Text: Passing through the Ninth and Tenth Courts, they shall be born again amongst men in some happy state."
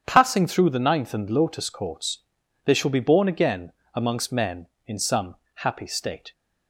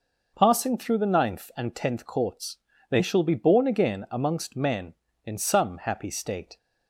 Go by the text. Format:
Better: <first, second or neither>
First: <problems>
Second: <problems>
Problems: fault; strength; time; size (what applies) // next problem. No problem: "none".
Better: second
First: starts louder than the rest; strong; until 1.0 s; 8 dB // says "Lotus" for "Tenth"; at 1.2 s // pauses between "again" and "amongst"; slight; at 3.7 s; 0.22 s long // pauses between "some" and "happy"; slight; at 5.3 s; 0.20 s long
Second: none